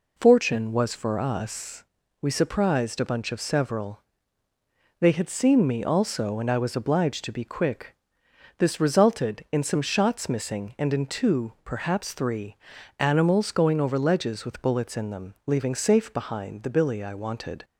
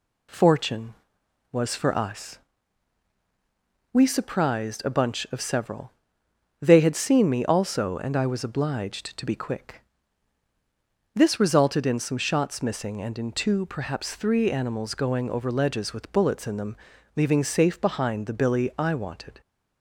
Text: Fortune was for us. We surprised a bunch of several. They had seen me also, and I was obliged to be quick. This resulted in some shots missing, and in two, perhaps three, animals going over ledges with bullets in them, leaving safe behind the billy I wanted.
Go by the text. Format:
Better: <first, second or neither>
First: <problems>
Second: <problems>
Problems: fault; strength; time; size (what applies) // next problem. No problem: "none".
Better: neither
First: none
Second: none